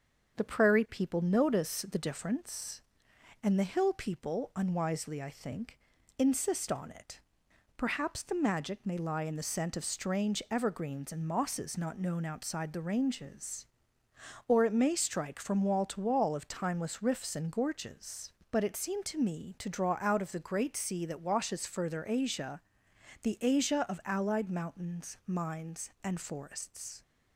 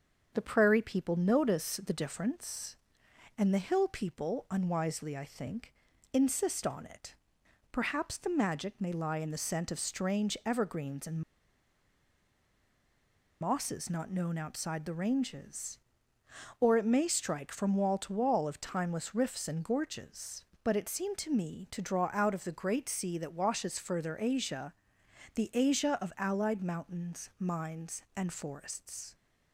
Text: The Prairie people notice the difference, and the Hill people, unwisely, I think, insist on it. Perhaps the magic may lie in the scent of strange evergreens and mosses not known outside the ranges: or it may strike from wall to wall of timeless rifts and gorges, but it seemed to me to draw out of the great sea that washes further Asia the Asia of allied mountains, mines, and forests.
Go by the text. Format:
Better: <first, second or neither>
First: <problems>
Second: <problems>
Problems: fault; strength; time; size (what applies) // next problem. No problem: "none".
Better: first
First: starts louder than the rest; until 1.4 s; 7 dB // pauses between "Asia" and "the"; noticeable; at 22.6 s; 0.62 s long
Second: starts louder than the rest; until 1.3 s; 7 dB // pauses between "and" and "mosses"; strong; at 11.2 s; 2.2 s long // pauses between "Asia" and "the"; noticeable; at 24.7 s; 0.62 s long